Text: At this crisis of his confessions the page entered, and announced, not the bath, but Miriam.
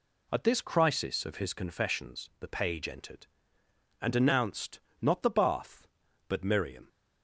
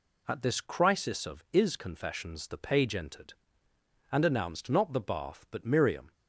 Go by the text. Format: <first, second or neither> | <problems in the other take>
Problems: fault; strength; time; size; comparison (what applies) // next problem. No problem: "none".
first | says "is" for "his"; at 1.5 s